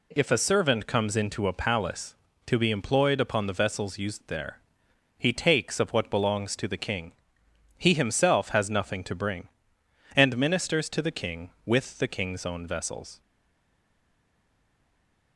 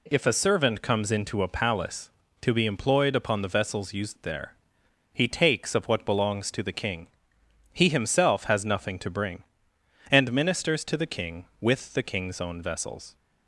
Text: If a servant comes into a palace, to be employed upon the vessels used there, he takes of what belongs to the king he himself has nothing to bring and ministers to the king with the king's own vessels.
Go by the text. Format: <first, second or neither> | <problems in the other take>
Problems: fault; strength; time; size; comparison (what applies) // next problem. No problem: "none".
second | pauses between "king" and "he"; noticeable; at 7.1 s; 0.66 s long; noticeable in the second // stays silent after the last word; from 13.2 s on; 2.1 s long